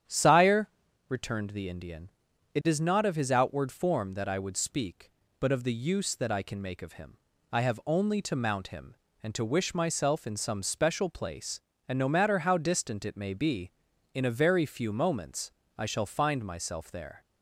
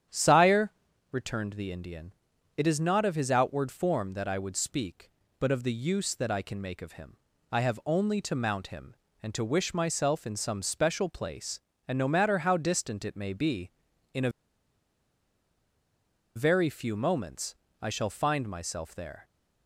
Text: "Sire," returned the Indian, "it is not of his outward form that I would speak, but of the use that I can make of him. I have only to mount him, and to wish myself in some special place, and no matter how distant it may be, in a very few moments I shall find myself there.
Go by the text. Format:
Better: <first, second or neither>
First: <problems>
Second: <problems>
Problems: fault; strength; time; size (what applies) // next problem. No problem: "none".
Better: first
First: starts louder than the rest; strong; until 1.4 s; 9.5 dB // pauses between "moments" and "I"; slight; at 15.5 s; 0.26 s long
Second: starts louder than the rest; strong; until 1.5 s; 9.5 dB // pauses between "a" and "very"; strong; at 14.2 s; 2.0 s long // pauses between "moments" and "I"; slight; at 17.5 s; 0.26 s long